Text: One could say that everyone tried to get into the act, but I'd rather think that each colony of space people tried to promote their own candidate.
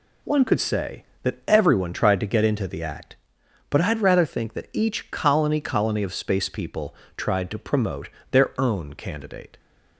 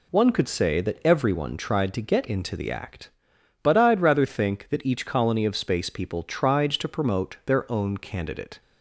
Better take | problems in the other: second | says "colony" twice; at 5.5 s // pauses between "people" and "tried"; slight; at 6.9 s; 0.22 s long // pauses between "promote" and "their"; slight; at 8.0 s; 0.24 s long

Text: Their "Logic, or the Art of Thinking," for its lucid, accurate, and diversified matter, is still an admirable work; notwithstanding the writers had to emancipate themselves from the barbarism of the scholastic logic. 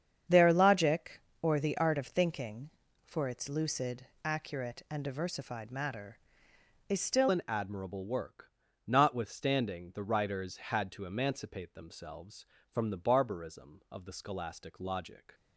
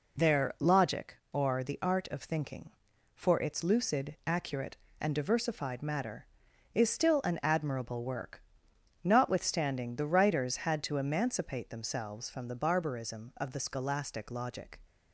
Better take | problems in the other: second | starts louder than the rest; strong; until 1.4 s; 7.5 dB // changes voice at "an"; from 7.2 s on; 8.1 s long

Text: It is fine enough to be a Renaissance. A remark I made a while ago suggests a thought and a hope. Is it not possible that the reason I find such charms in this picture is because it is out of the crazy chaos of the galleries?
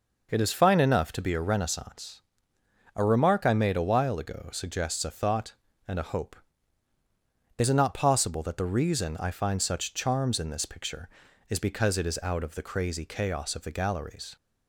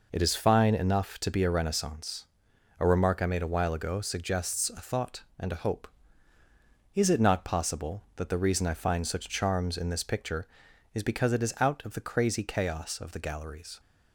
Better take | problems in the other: neither | none

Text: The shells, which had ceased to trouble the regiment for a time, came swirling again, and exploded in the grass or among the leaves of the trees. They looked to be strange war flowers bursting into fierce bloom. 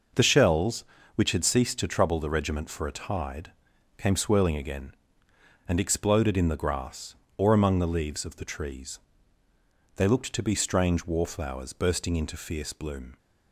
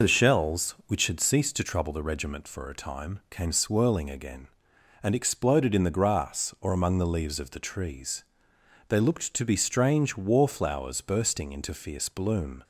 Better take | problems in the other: second | says "tide" for "time"; at 2.9 s

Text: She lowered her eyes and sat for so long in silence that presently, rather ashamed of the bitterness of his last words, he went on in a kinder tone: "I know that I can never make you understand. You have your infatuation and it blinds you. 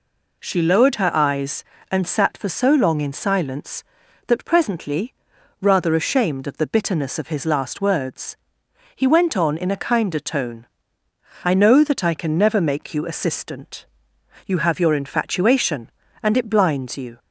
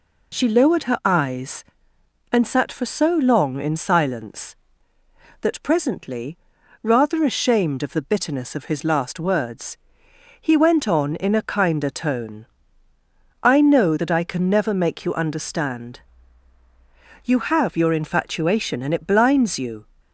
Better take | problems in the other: second | says "assistant" for "understand"; at 13.0 s

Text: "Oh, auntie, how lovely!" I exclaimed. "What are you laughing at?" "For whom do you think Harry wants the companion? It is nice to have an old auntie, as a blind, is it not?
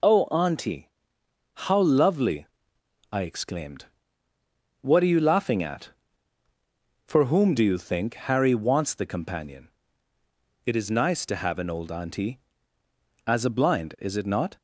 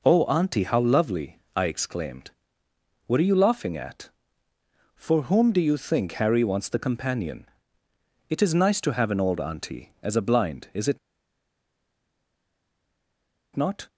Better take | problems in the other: first | pauses between "it" and "not"; strong; at 10.9 s; 2.5 s long

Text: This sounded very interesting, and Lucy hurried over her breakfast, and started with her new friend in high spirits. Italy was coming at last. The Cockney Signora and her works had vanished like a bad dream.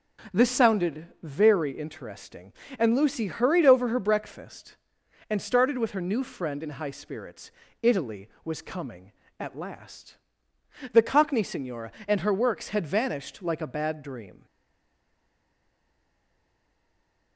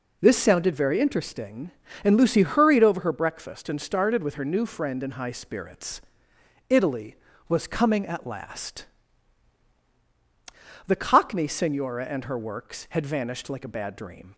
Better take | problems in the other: second | stays silent after the last word; strong; from 14.4 s on; 2.9 s long

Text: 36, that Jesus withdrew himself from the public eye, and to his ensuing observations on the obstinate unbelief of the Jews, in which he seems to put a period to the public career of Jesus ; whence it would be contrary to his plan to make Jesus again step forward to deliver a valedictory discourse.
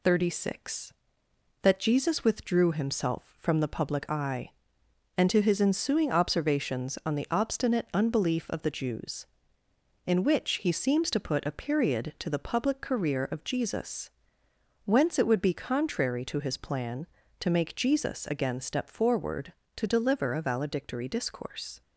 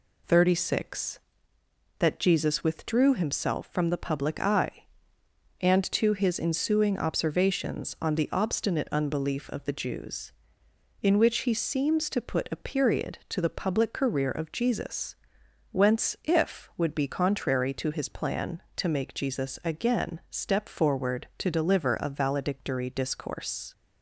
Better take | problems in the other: first | says "if" for "it"; at 16.2 s

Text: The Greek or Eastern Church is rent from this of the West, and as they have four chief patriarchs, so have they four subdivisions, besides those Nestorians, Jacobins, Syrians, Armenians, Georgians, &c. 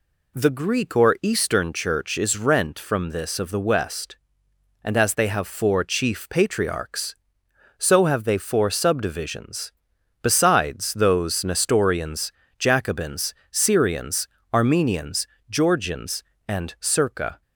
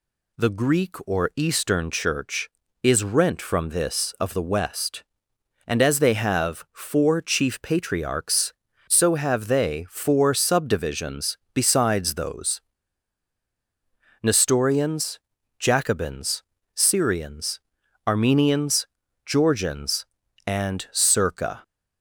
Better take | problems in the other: first | pauses between "those" and "Nestorians"; strong; at 12.6 s; 1.6 s long

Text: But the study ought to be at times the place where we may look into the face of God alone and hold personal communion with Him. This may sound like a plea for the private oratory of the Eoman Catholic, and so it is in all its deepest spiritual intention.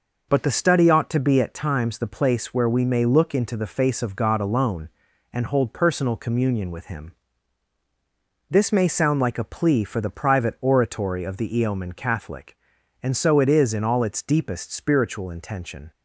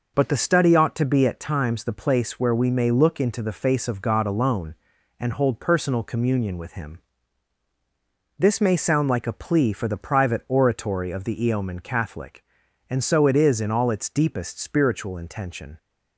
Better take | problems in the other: neither | none

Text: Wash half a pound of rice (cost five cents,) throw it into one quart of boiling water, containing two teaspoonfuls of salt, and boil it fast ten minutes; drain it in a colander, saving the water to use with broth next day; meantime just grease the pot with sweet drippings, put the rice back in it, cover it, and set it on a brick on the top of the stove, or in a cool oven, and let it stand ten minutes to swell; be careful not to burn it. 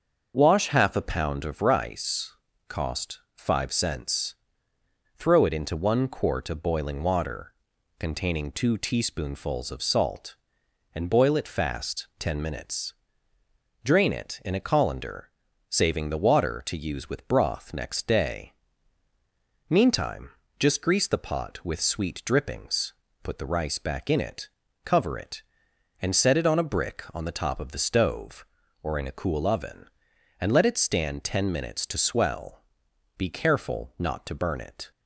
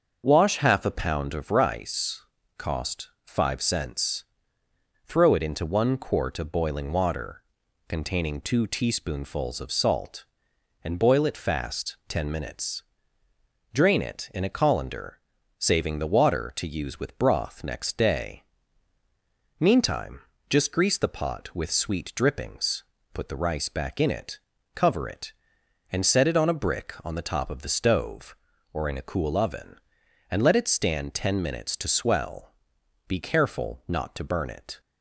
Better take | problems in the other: neither | starts louder than the rest; the same in both // pauses between "cost" and "five"; slight; the same in both // pauses between "meantime" and "just"; slight; the same in both

